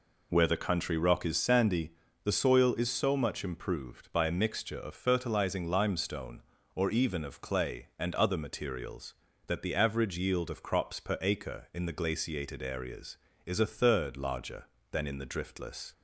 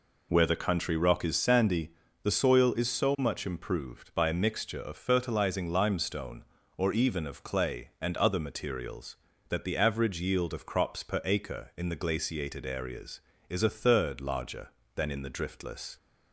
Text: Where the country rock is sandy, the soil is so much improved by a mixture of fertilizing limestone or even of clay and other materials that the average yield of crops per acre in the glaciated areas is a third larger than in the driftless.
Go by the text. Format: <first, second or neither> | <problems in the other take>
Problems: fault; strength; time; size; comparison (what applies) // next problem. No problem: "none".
neither | none